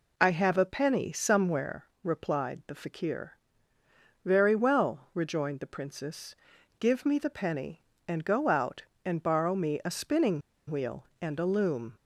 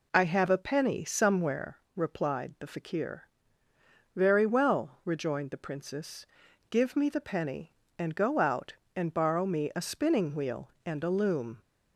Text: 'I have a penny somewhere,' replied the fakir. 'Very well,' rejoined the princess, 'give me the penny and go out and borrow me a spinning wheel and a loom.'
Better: second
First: pauses between "spinning" and "wheel"; slight; at 10.4 s; 0.30 s long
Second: none

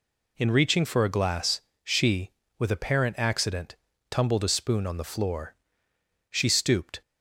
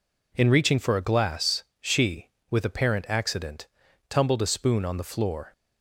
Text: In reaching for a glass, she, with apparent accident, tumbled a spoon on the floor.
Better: second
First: goes on to say "She stooped"; noticeable; from 6.2 s on; 0.72 s long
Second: none

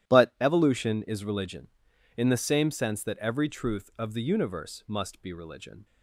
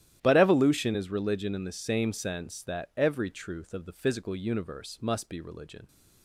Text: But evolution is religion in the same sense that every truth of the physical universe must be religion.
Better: second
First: starts louder than the rest; strong; until 1.1 s; 12 dB // skips "physical"; at 4.2 s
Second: starts louder than the rest; strong; until 1.2 s; 12.5 dB

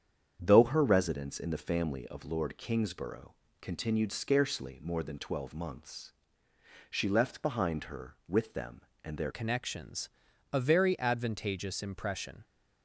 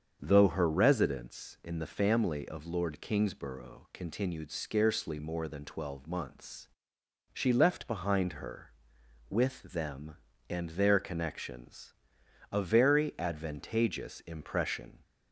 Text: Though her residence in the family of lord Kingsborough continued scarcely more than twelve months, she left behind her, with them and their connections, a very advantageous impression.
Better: second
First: starts louder than the rest; strong; until 1.4 s; 8 dB // pauses between "Kingsborough" and "continued"; slight; at 3.3 s; 0.26 s long // changes voice at "connections"; from 9.3 s on; 3.1 s long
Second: starts louder than the rest; strong; until 1.2 s; 7 dB

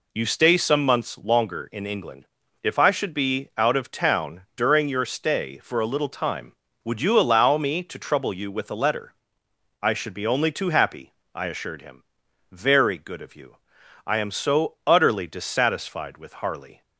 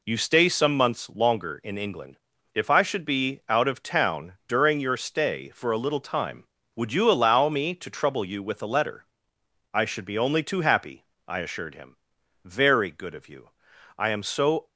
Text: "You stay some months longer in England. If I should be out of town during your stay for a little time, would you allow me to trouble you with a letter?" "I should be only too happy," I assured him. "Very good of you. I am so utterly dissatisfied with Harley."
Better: first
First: pauses between "town" and "during"; slight; at 4.4 s; 0.16 s long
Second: pauses between "town" and "during"; slight; at 4.3 s; 0.16 s long // stops before "utterly dissatisfied with Harley"; at 14.6 s

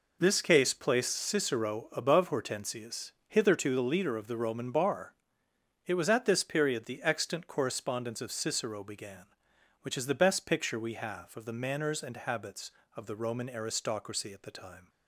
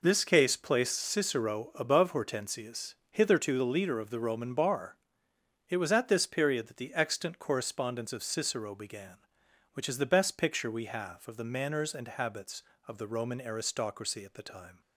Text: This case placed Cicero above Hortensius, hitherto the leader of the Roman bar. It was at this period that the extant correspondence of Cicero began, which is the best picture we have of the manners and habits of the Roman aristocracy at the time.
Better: second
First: skips "that"; at 6.8 s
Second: none

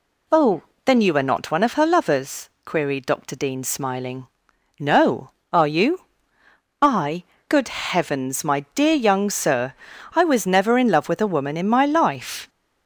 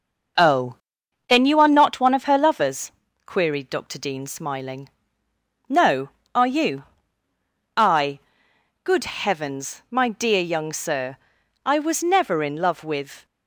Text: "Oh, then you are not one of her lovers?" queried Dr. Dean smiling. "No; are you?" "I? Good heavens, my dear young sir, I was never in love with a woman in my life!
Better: first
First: none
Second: starts louder than the rest; noticeable; until 1.9 s; 6 dB // stops before "a woman in my life"; at 13.2 s

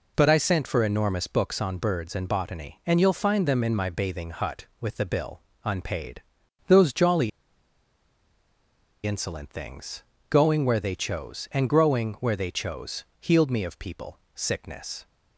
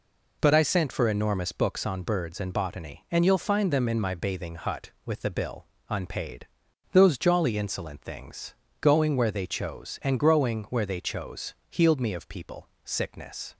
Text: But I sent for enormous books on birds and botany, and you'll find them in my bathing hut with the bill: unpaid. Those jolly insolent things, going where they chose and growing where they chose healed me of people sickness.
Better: second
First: pauses between "jolly" and "insolent"; strong; at 7.2 s; 1.7 s long // pauses between "people" and "sickness"; slight; at 14.1 s; 0.16 s long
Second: pauses between "people" and "sickness"; slight; at 12.6 s; 0.16 s long

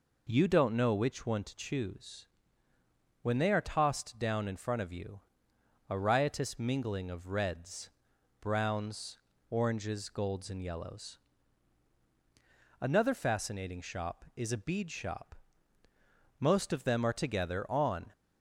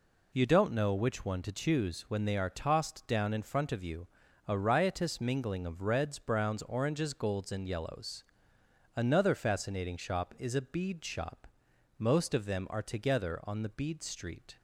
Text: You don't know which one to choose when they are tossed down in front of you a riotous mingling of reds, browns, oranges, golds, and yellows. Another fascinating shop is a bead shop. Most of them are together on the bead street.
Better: second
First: pauses between "choose" and "when"; noticeable; at 2.2 s; 0.96 s long // pauses between "you" and "a"; noticeable; at 5.1 s; 0.68 s long // stops before "the bead street"; at 18.1 s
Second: pauses between "you" and "a"; at 4.0 s; 0.42 s long

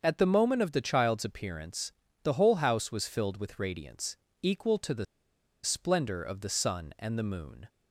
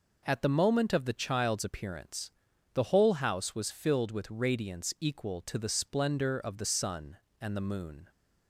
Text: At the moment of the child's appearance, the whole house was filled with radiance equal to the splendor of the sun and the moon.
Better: second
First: starts louder than the rest; until 1.0 s; 7 dB // pauses between "radiance" and "equal"; slight; at 4.1 s; 0.28 s long // pauses between "the" and "splendor"; noticeable; at 5.0 s; 0.59 s long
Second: none

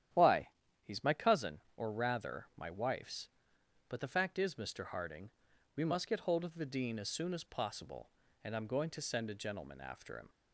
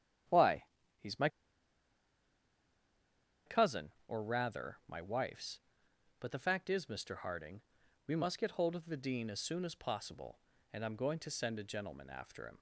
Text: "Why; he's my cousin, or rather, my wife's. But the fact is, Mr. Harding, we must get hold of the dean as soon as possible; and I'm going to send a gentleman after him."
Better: first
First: starts louder than the rest; strong; until 1.4 s; 10.5 dB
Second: starts louder than the rest; strong; until 3.8 s; 10.5 dB // pauses between "my" and "cousin"; strong; at 1.2 s; 2.1 s long

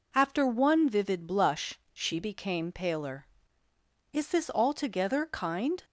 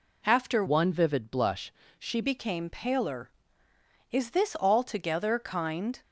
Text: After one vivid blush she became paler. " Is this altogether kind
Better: first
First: none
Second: changes voice from "one" to "she"; from 0.6 to 2.2 s; 1.6 s long // pauses between "blush" and "she"; slight; at 1.7 s; 0.26 s long

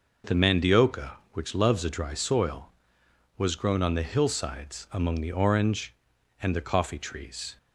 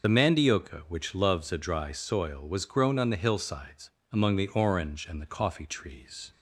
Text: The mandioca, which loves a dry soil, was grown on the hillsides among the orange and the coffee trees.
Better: first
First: none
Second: loses the start of "The"; at 0.0 s; 30 ms // pauses between "hillsides" and "among"; slight; at 3.8 s; 0.24 s long

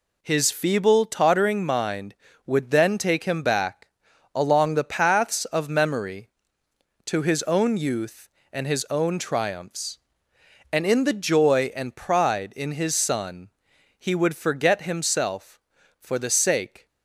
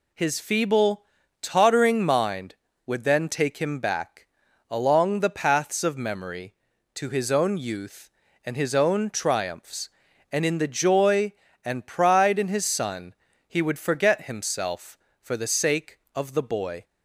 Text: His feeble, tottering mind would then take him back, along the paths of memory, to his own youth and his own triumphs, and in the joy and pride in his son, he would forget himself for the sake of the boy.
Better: second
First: stops before "of the boy"; at 16.8 s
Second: none

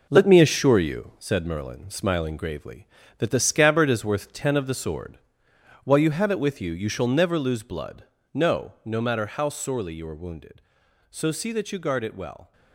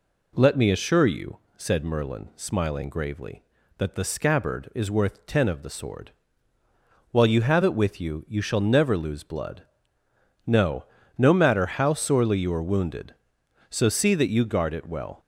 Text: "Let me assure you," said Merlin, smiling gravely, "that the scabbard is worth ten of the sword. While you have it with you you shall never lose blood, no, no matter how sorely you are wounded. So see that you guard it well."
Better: second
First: gets quieter; strong; throughout; 7.5 dB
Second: none

